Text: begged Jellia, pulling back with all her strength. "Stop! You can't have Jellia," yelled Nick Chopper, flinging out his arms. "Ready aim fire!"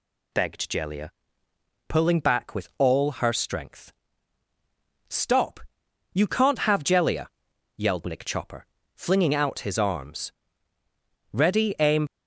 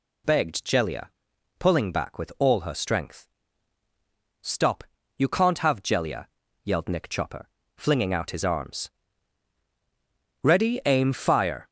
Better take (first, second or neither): second